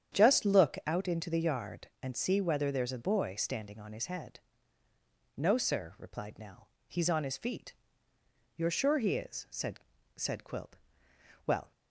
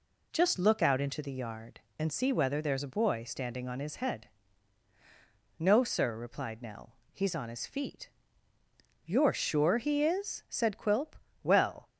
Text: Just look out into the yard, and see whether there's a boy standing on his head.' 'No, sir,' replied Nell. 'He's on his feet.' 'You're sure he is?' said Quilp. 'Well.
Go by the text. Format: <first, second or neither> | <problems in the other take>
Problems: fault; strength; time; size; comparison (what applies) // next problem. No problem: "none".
second | starts louder than the rest; strong; until 1.2 s; 9 dB // says "said" twice; at 10.1 s